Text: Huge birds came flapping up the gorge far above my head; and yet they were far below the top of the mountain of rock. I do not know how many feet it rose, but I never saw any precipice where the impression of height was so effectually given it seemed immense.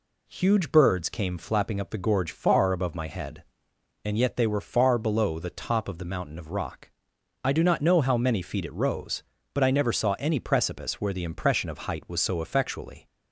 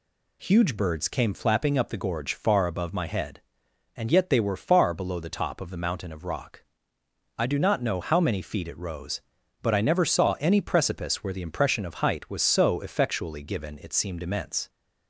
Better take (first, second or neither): second